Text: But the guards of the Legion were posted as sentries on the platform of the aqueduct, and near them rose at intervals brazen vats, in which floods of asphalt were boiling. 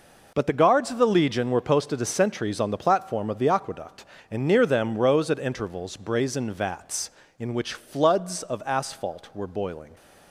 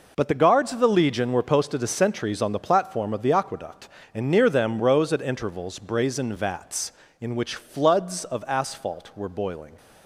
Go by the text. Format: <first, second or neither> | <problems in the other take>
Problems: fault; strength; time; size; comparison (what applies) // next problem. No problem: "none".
neither | none